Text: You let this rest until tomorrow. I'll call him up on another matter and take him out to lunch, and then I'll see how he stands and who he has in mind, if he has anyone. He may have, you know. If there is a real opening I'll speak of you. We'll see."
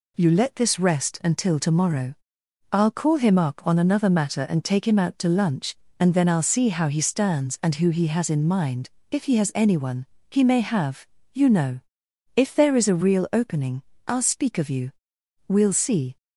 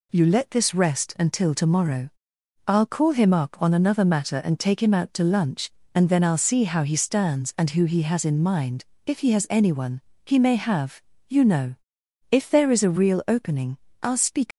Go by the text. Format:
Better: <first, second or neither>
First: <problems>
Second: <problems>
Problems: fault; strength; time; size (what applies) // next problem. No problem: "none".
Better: first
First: pauses between "opening" and "I'll"; slight; at 13.8 s; 0.24 s long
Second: pauses between "opening" and "I'll"; slight; at 13.7 s; 0.24 s long // stops before "of you We'll see"; at 14.5 s